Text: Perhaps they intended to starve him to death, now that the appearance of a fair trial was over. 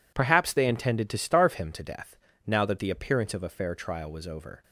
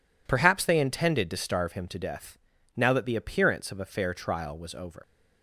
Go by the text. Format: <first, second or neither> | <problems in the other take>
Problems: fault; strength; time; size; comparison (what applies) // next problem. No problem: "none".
first | leaves "over" unfinished; at 5.0 s; 130 ms